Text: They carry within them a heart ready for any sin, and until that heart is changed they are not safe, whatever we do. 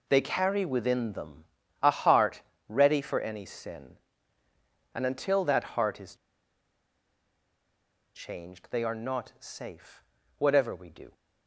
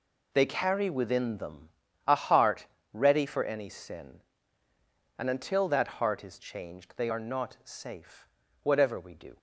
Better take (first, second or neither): second